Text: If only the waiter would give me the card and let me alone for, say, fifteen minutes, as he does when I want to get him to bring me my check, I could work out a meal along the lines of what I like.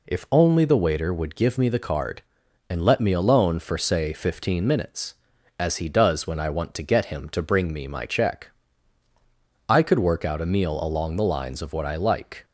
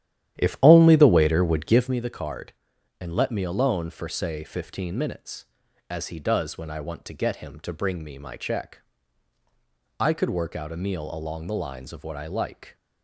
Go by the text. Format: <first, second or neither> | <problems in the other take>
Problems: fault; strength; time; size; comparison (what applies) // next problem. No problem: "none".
first | starts louder than the rest; strong; until 1.9 s; 11.5 dB